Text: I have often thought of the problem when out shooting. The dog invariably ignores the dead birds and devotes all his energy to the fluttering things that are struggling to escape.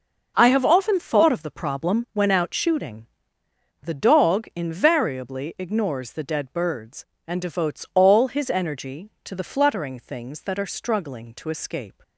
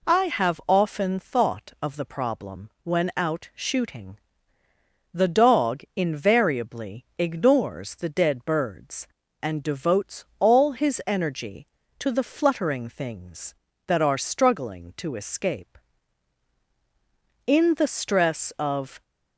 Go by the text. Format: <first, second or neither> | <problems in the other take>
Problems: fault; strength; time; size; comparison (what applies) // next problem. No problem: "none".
first | pauses between "devotes" and "all"; slight; at 10.2 s; 0.16 s long // goes on to say "In the stress of"; from 17.4 s on; 1.5 s long